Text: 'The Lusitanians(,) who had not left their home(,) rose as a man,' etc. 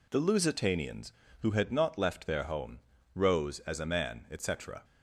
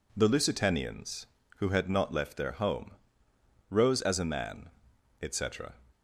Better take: neither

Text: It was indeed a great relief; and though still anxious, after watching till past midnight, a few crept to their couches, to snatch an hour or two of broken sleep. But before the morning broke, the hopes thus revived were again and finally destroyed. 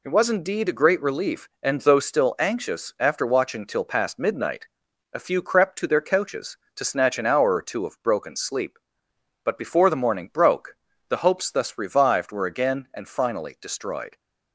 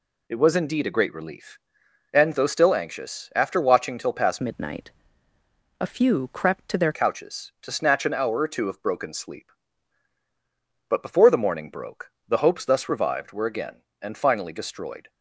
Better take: first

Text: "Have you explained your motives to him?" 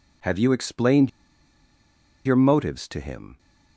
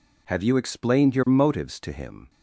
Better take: second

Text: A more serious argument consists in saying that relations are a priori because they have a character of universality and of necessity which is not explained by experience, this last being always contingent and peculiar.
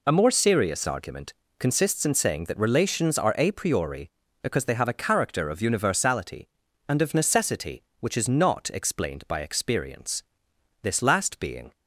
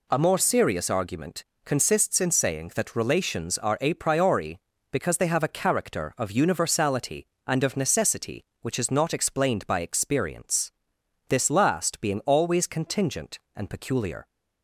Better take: second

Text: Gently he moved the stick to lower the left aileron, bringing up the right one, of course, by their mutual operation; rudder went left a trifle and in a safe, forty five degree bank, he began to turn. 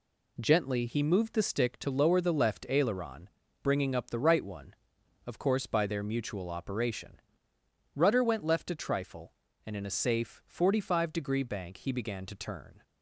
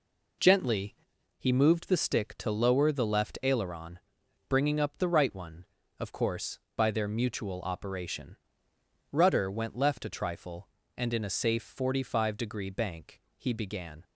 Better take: first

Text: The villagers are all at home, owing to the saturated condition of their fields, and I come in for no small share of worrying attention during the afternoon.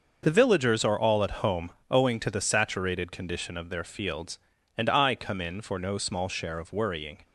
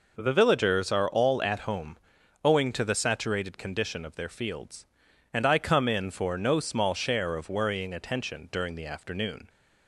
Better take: second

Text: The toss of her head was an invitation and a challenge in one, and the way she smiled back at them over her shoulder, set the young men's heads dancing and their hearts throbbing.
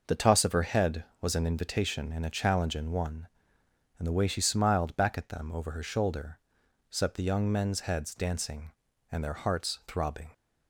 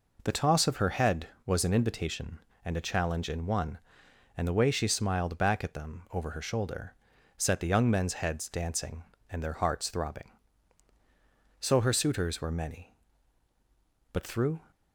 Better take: first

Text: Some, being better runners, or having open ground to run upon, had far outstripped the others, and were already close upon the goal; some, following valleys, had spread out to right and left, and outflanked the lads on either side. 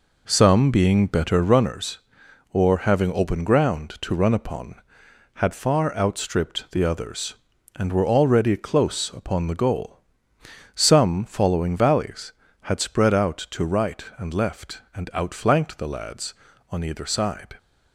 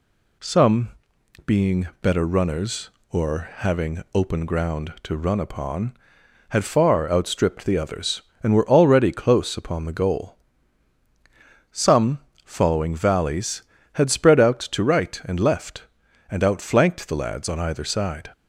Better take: second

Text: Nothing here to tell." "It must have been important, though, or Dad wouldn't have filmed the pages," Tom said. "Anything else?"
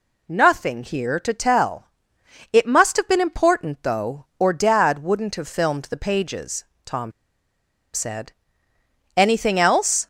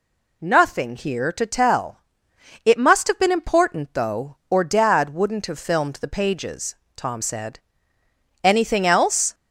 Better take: second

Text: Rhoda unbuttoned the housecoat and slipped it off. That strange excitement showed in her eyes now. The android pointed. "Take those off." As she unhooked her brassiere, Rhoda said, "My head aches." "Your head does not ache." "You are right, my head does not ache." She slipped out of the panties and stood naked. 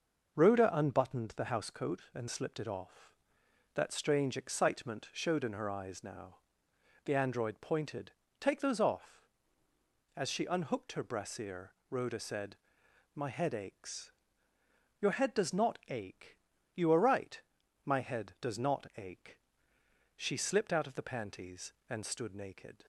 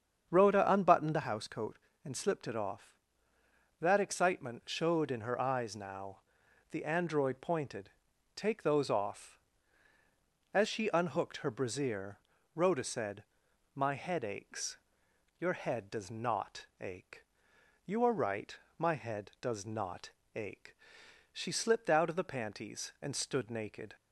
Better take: first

